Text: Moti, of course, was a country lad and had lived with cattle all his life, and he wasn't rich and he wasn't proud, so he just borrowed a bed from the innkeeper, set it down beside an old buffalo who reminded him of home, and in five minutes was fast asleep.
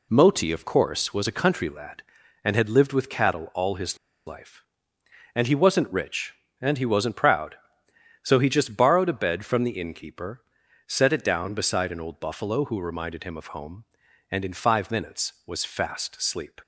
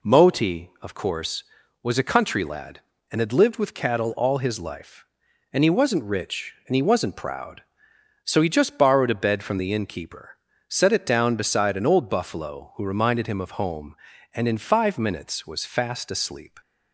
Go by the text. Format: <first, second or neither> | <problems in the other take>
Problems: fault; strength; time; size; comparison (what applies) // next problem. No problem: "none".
second | pauses between "his" and "life"; slight; at 3.9 s; 0.30 s long